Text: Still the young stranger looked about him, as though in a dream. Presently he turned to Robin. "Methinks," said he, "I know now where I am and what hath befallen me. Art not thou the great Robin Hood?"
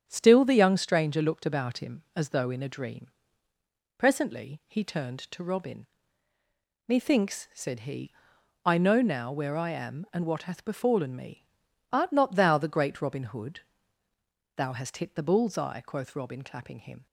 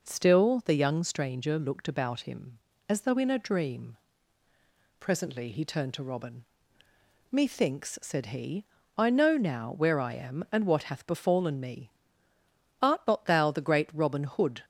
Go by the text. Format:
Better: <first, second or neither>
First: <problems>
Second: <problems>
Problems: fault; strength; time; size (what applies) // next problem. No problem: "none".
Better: second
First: starts louder than the rest; strong; until 1.0 s; 9 dB // goes on to say "Thou hast hit the bull's eye quoth Robin clapping him"; strong; from 14.5 s on; 2.5 s long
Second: none